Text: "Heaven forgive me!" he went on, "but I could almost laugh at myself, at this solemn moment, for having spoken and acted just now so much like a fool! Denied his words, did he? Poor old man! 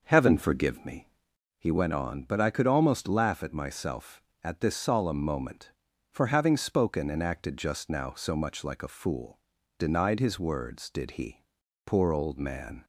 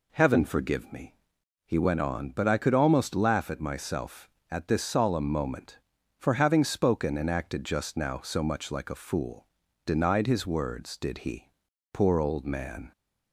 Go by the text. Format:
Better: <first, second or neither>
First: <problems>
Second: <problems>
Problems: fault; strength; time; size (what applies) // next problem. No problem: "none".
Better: second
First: starts louder than the rest; noticeable; until 1.5 s; 6 dB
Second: none